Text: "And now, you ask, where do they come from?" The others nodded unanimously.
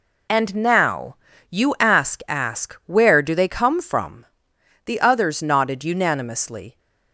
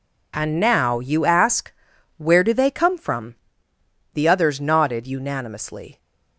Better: second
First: says "ask" twice; at 2.2 s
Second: none

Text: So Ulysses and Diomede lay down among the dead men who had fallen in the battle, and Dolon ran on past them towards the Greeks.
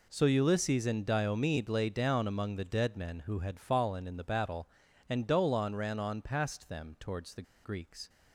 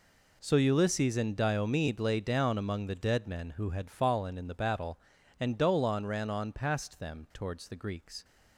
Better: second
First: pauses between "the" and "Greeks"; slight; at 7.4 s; 0.21 s long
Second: none

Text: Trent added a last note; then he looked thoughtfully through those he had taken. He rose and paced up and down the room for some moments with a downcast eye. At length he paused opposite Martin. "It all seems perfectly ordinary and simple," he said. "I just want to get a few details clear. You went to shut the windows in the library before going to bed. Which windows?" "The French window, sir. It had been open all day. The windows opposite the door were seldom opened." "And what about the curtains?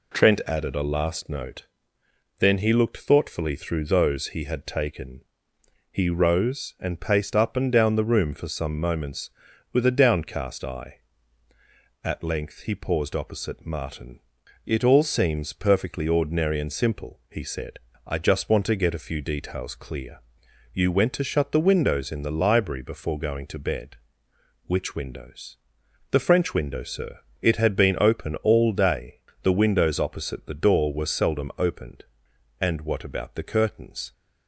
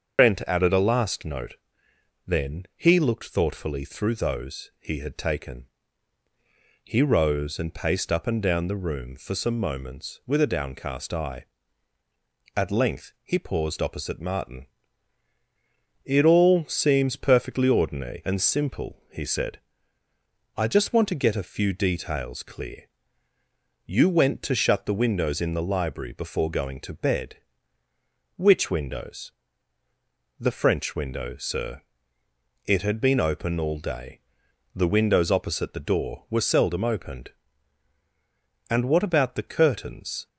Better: first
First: none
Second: loses the start of "Trent"; at 0.1 s; 120 ms // starts louder than the rest; until 1.2 s; 7 dB

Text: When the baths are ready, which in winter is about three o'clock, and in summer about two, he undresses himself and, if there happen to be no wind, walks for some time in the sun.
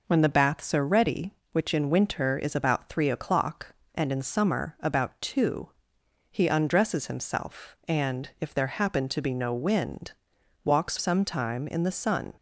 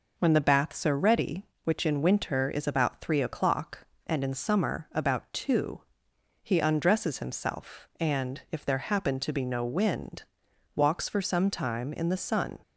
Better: second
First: skips "for"; at 10.9 s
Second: none

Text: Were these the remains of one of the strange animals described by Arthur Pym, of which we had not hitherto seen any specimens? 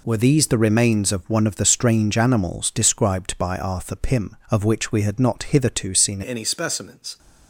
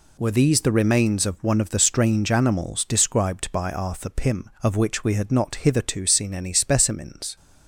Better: second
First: changes voice at "any"; from 6.2 s on; 0.9 s long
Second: none

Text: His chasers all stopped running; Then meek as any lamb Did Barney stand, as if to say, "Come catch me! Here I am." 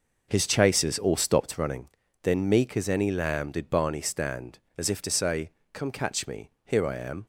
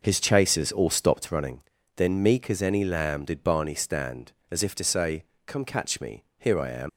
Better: first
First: none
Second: leaves "am" unfinished; at 6.8 s; 95 ms

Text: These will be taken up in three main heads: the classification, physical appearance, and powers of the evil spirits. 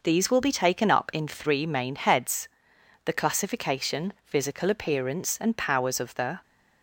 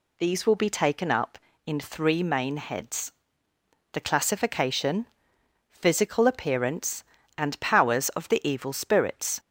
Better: second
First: stops before "evil spirits"; at 6.4 s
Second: none

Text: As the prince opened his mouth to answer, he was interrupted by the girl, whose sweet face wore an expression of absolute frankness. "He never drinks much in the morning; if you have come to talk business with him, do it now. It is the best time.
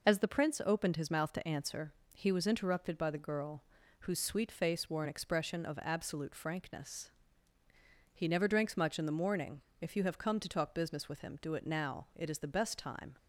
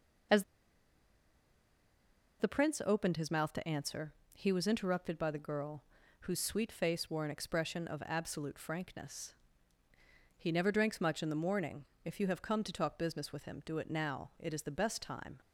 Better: first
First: none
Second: pauses between "As" and "the"; strong; at 0.4 s; 1.9 s long

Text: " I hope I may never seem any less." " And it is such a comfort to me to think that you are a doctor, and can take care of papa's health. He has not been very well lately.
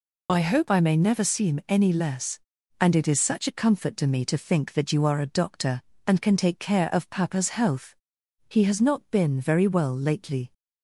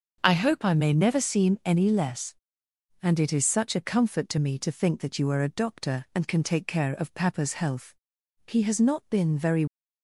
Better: first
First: none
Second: starts louder than the rest; until 1.2 s; 6 dB // stops before "well lately"; at 9.6 s

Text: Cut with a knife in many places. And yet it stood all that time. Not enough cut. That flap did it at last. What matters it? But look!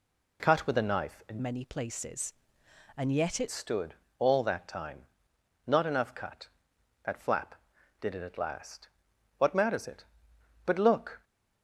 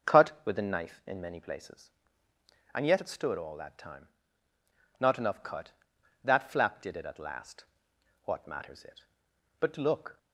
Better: second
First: changes voice from "many" to "it"; from 1.4 to 3.4 s; 2.0 s long // pauses between "stood" and "all"; slight; at 3.9 s; 0.26 s long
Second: none

